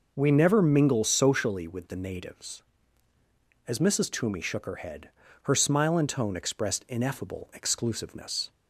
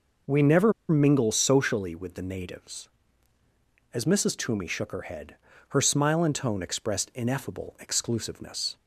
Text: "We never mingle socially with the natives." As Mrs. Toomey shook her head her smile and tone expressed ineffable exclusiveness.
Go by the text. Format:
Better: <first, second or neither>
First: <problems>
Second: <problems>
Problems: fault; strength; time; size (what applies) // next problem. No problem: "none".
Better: first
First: pauses between "head" and "her"; slight; at 5.0 s; 0.36 s long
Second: pauses between "never" and "mingle"; slight; at 0.7 s; 0.17 s long // pauses between "head" and "her"; slight; at 5.3 s; 0.36 s long